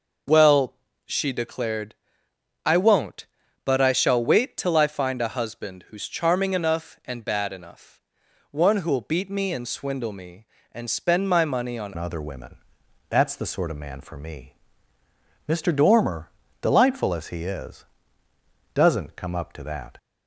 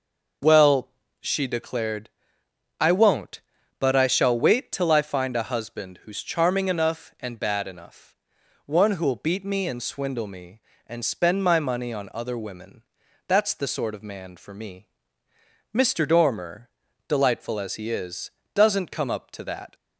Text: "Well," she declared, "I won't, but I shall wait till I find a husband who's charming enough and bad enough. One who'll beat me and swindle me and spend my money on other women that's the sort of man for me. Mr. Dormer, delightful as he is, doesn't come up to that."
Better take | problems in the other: second | changes voice at "other"; from 11.9 s on; 8.0 s long // pauses between "women" and "that's"; noticeable; at 12.5 s; 0.54 s long; also in the second

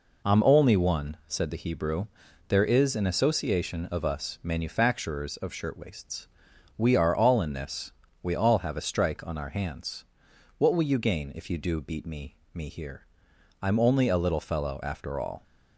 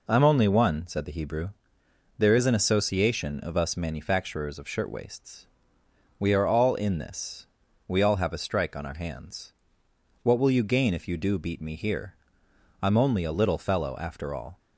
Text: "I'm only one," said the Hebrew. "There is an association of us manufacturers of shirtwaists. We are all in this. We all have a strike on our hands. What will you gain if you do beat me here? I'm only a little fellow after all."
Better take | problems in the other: second | says "me" twice; at 12.5 s

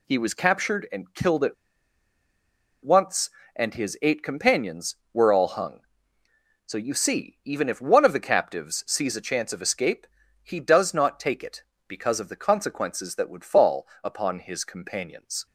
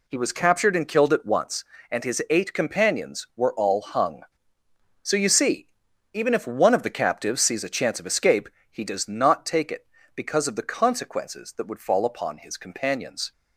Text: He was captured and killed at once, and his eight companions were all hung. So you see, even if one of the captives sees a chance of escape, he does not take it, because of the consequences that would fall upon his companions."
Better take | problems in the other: second | pauses between "at" and "once"; strong; at 1.5 s; 1.3 s long // pauses between "fall" and "upon"; slight; at 13.8 s; 0.18 s long

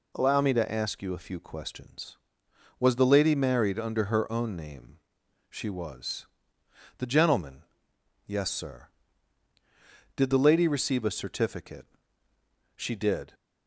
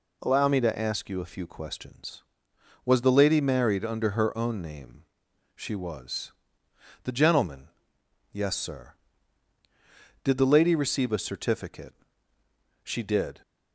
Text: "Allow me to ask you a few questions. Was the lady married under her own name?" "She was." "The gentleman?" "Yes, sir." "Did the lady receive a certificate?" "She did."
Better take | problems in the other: neither | none

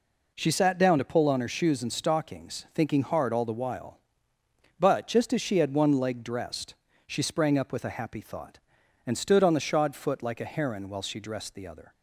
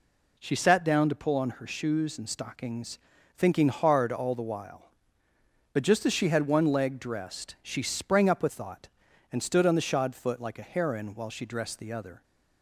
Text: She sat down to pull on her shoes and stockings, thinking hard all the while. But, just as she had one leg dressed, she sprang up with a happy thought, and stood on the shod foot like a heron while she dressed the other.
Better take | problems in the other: first | skips "a happy"; at 8.4 s

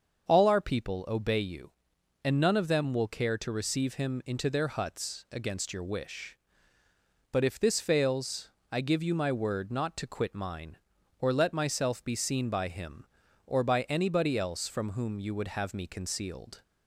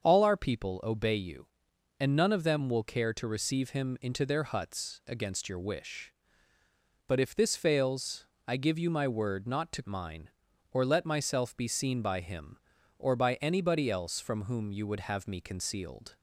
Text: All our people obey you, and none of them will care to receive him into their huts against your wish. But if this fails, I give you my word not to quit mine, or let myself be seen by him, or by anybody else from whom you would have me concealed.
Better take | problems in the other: first | starts louder than the rest; until 1.0 s; 6.5 dB; also in the first // skips "quit"; at 9.8 s

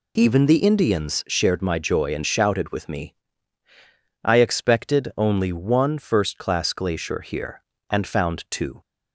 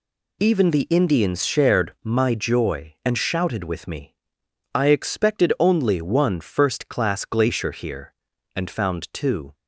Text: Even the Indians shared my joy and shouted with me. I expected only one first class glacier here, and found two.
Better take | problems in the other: neither | none

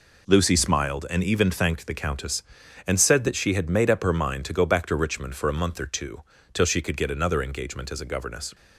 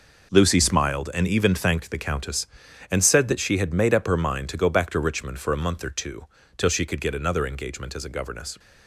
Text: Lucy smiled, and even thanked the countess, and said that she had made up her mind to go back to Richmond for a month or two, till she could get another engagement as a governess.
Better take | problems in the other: first | gets quieter; strong; throughout; 11 dB

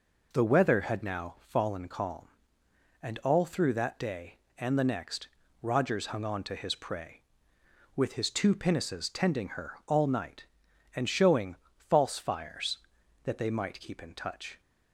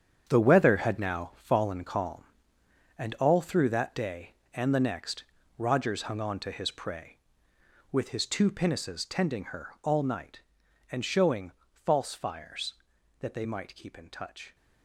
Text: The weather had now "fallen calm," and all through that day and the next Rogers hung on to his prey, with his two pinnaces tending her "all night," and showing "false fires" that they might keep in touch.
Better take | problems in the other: first | gets quieter; strong; throughout; 11 dB // pauses between "next" and "Rogers"; slight; at 5.2 s; 0.34 s long; slight in the first // pauses between "showing" and "false"; slight; at 11.5 s; 0.18 s long; slight in the first

